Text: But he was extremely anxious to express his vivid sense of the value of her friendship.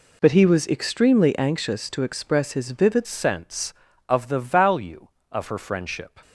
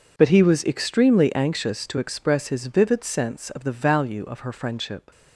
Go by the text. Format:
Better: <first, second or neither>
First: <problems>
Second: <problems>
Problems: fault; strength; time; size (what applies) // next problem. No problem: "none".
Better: second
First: changes voice at "sense"; from 3.0 s on; 3.1 s long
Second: none